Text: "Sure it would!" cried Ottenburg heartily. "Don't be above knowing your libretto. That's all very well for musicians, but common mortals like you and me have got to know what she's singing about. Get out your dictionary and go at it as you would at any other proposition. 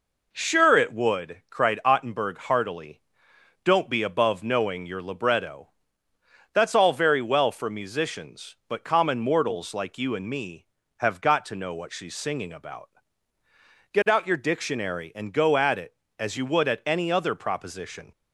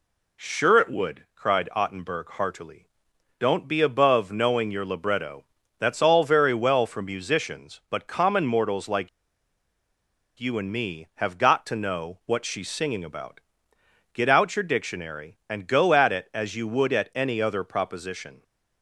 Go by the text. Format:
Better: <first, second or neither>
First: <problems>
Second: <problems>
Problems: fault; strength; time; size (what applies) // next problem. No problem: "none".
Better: first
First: none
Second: pauses between "like" and "you"; strong; at 9.0 s; 1.2 s long